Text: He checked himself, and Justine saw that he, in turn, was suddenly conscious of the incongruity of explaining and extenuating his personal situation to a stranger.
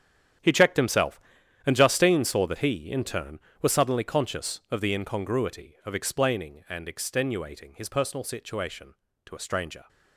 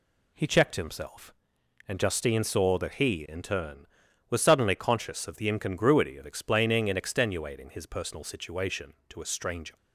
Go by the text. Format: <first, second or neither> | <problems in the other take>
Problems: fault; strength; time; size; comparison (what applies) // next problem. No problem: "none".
second | gets quieter; strong; throughout; 13 dB